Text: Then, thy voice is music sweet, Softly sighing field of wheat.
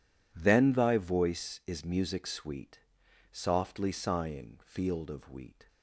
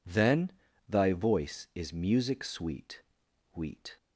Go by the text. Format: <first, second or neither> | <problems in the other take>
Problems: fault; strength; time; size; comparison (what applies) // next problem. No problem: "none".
first | skips "Softly sighing field of"; at 3.2 s